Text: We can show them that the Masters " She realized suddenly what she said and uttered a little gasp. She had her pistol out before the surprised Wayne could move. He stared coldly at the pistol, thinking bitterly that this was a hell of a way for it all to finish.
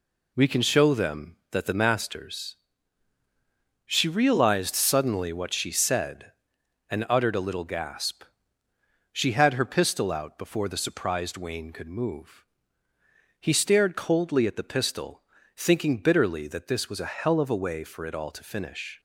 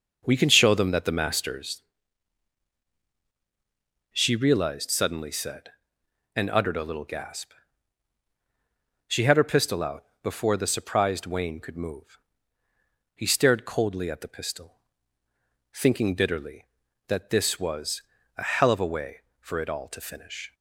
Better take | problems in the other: first | starts louder than the rest; noticeable; until 1.3 s; 6 dB // skips "what she"; at 5.2 s // pauses between "out" and "before"; slight; at 10.0 s; 0.18 s long // pauses between "was" and "a"; slight; at 18.0 s; 0.36 s long

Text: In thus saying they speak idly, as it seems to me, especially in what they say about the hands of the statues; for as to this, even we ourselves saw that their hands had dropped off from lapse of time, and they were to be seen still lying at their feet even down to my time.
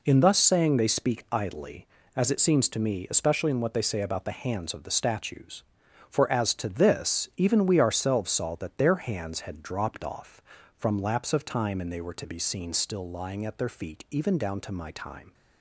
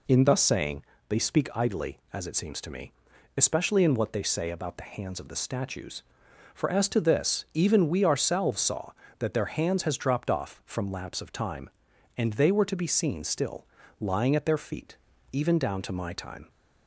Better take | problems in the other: first | pauses between "saying" and "they"; slight; at 0.8 s; 0.24 s long // says "has" for "had"; at 9.8 s // pauses between "still" and "lying"; slight; at 13.6 s; 0.34 s long // pauses between "feet" and "even"; slight; at 14.9 s; 0.36 s long

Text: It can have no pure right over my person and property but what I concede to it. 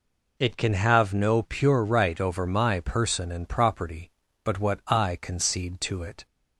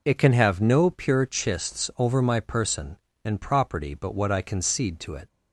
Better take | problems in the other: first | says "chists" for "right"; at 1.2 s

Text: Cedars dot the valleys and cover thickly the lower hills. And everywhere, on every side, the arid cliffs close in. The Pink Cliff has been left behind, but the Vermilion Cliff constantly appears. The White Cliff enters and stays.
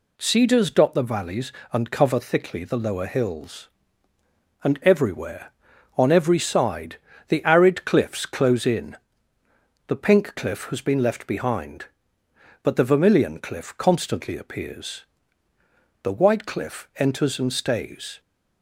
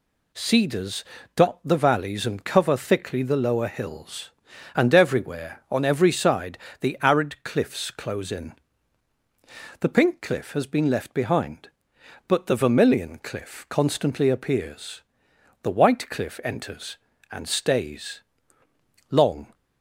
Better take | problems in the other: first | pauses between "Cedars" and "dot"; slight; at 1.0 s; 0.32 s long // goes on to say "Long"; slight; from 19.1 s on; 0.42 s long

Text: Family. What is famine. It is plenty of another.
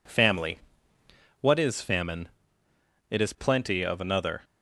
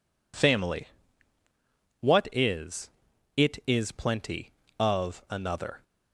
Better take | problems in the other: first | skips "famine"; at 3.1 s

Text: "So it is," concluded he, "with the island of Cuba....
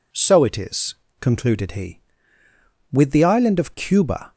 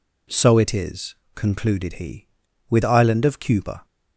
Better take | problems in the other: first | skips "the"; at 2.8 s

